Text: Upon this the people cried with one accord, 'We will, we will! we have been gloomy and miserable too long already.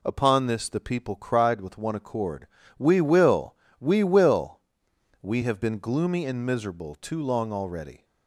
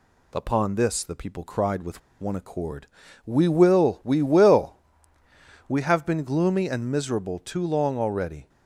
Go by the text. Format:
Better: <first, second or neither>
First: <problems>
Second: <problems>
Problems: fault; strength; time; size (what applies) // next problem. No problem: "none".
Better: first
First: none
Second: pauses between "with" and "one"; slight; at 2.0 s; 0.20 s long